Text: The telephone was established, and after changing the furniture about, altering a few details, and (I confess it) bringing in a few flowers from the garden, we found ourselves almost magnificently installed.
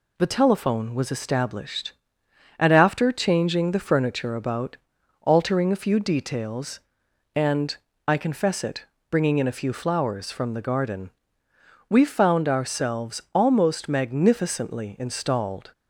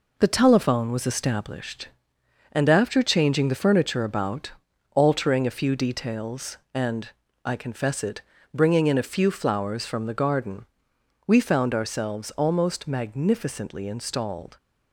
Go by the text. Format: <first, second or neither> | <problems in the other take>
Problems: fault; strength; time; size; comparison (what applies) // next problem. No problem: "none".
first | gets quieter; noticeable; throughout; 6 dB